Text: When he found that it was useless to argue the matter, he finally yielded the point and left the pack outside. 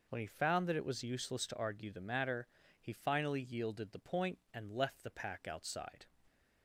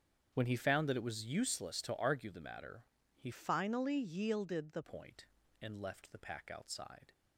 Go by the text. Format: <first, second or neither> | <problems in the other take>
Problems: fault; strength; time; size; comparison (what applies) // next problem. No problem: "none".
first | starts louder than the rest; strong; until 1.3 s; 7.5 dB // changes voice from "finally" to "the"; from 3.3 to 4.8 s; 1.5 s long